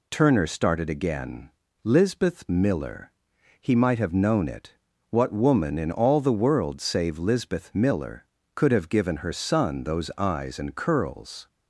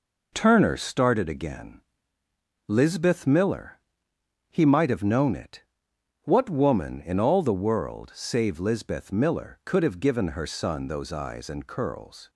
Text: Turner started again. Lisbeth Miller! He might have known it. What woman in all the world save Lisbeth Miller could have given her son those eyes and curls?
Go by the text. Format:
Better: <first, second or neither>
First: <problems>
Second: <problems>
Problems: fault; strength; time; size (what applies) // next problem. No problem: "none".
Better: neither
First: none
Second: none